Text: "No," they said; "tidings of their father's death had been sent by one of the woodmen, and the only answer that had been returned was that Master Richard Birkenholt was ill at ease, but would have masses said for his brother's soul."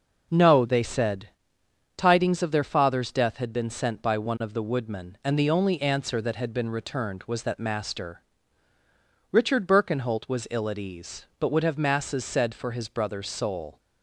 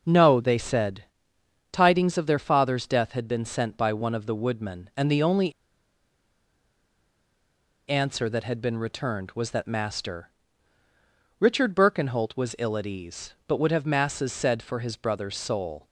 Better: first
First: pauses between "Master" and "Richard"; at 8.2 s; 1.1 s long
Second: pauses between "only" and "answer"; strong; at 5.5 s; 2.3 s long // pauses between "Master" and "Richard"; at 10.2 s; 1.1 s long

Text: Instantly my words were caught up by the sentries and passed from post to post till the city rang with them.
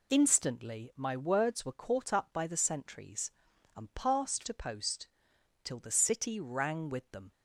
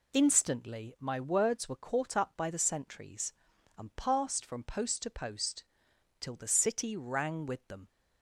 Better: second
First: skips "from post"; at 4.4 s // pauses between "post" and "till"; noticeable; at 5.0 s; 0.58 s long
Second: pauses between "post" and "till"; noticeable; at 5.6 s; 0.58 s long

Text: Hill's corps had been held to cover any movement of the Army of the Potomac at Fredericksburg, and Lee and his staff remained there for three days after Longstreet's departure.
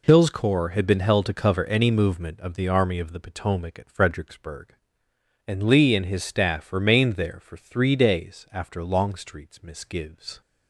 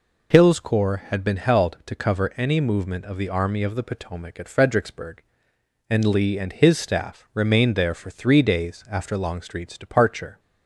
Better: second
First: says "misgives" for "departure"; at 9.6 s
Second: none

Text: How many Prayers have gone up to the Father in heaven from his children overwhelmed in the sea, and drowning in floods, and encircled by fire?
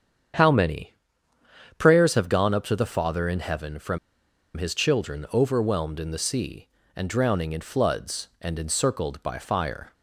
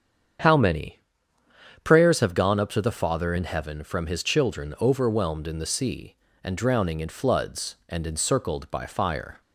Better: second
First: starts louder than the rest; strong; until 2.2 s; 8 dB // pauses between "many" and "Prayers"; noticeable; at 0.9 s; 0.88 s long // pauses between "from" and "his"; noticeable; at 3.9 s; 0.58 s long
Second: starts louder than the rest; strong; until 2.2 s; 8 dB // pauses between "many" and "Prayers"; noticeable; at 0.9 s; 0.88 s long

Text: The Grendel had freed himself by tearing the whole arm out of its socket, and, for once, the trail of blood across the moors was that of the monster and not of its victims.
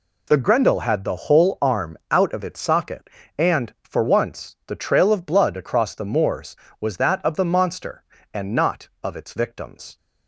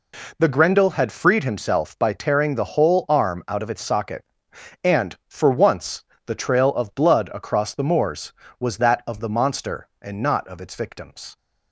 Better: second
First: skips "freed himself by tearing"; at 1.0 s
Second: none

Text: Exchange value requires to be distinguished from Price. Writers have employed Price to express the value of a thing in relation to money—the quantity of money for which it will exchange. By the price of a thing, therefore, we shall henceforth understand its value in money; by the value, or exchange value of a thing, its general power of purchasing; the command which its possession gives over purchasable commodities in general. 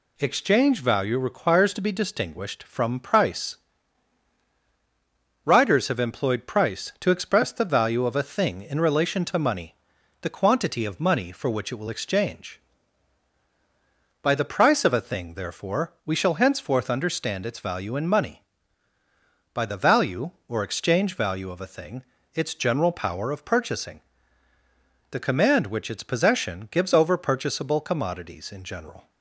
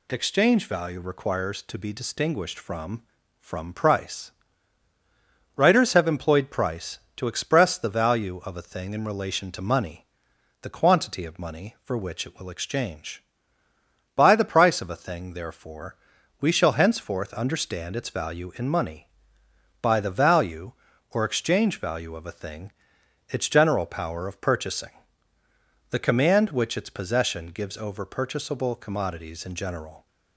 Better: first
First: none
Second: says "from" twice; at 3.3 s

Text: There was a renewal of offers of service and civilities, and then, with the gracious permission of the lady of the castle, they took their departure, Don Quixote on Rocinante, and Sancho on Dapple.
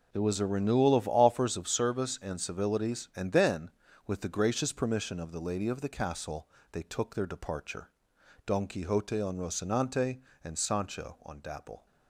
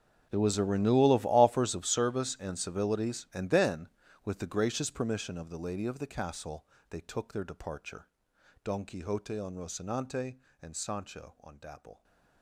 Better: first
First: none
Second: gets quieter; strong; throughout; 18.5 dB

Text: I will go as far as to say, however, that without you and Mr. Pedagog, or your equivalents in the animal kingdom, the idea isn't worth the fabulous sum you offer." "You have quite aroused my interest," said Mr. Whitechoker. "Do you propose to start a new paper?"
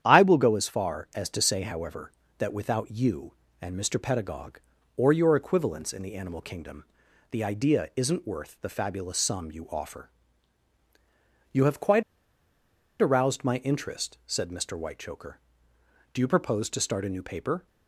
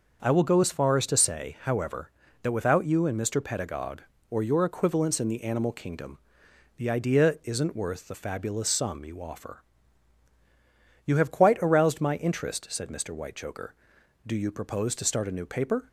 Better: second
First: starts louder than the rest; strong; until 1.0 s; 9.5 dB // pauses between "quite" and "aroused"; at 12.0 s; 0.98 s long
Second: starts louder than the rest; until 1.2 s; 6 dB

